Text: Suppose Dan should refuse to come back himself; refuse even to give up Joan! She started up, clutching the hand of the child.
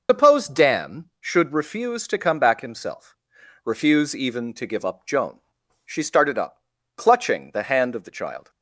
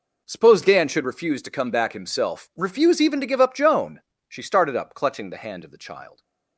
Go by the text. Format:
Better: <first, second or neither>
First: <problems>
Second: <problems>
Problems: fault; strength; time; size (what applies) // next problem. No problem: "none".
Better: second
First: loses the start of "Suppose"; at 0.0 s; 115 ms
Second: none